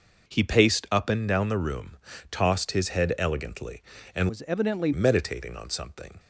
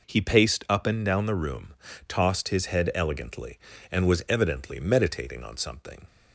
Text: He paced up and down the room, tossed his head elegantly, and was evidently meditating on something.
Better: second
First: changes voice from "was" to "evidently"; from 4.2 to 4.9 s; 0.7 s long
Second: none

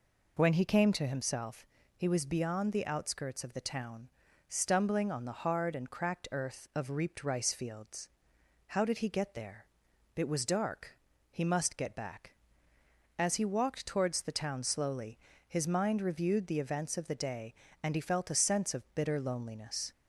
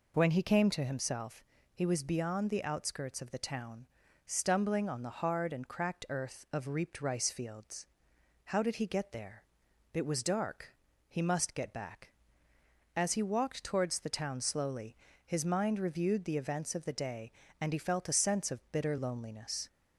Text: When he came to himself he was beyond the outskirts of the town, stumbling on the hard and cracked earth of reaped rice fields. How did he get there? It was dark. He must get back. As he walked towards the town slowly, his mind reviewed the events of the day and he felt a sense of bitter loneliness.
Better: neither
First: pauses between "himself" and "he"; slight; at 1.6 s; 0.30 s long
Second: pauses between "himself" and "he"; slight; at 1.4 s; 0.30 s long

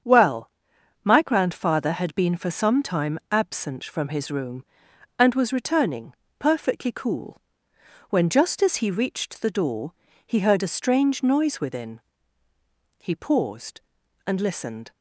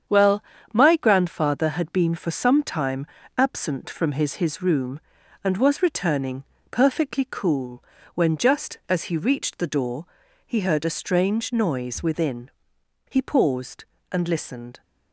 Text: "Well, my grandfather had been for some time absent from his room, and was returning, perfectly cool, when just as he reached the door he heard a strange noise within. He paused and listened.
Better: first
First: starts louder than the rest; strong; until 1.5 s; 7 dB // pauses between "door" and "he"; slight; at 9.9 s; 0.32 s long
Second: starts louder than the rest; strong; until 1.3 s; 8 dB // pauses between "time" and "absent"; slight; at 3.0 s; 0.30 s long // says "his" twice; at 4.3 s // pauses between "door" and "he"; at 10.0 s; 0.40 s long

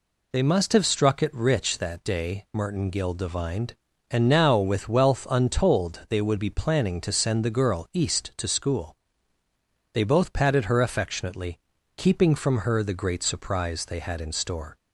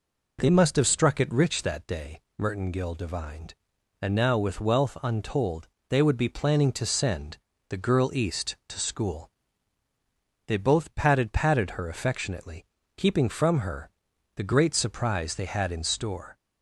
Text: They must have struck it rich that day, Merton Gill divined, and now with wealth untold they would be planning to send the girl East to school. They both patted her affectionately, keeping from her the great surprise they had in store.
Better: first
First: none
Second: pauses between "untold" and "they"; slight; at 5.6 s; 0.22 s long // pauses between "send" and "the"; slight; at 7.3 s; 0.32 s long // says "patted" twice; at 11.3 s // pauses between "her" and "the"; noticeable; at 13.9 s; 0.46 s long

